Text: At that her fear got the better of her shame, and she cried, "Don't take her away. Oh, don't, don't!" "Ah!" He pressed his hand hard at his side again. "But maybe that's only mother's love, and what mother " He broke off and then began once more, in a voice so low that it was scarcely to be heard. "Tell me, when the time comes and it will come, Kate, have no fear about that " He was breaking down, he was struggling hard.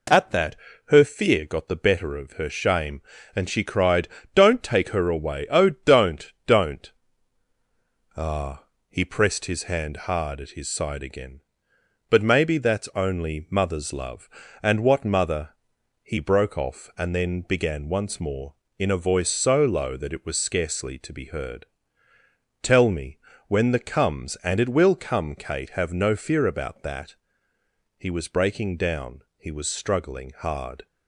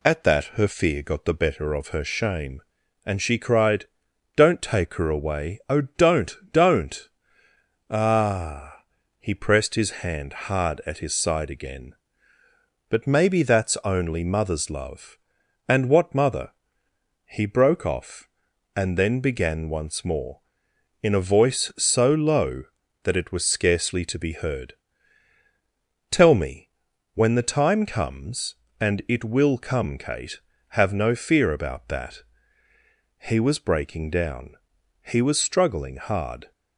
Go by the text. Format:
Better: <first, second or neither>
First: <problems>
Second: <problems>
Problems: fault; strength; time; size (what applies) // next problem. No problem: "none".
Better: second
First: pauses between "that" and "her"; slight; at 0.5 s; 0.30 s long // skips "time"; at 23.7 s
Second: none